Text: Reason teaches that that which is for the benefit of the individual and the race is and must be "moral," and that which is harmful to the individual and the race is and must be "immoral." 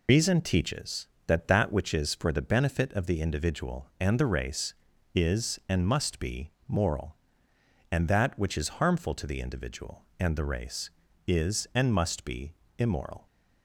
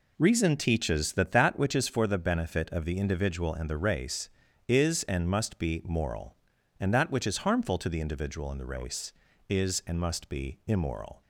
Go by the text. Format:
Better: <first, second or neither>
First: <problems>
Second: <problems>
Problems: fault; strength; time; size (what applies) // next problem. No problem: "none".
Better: second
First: loses the start of "Reason"; at 0.0 s; 95 ms // pauses between "be" and "moral"; slight; at 6.4 s; 0.18 s long // pauses between "be" and "immoral"; slight; at 12.5 s; 0.24 s long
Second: none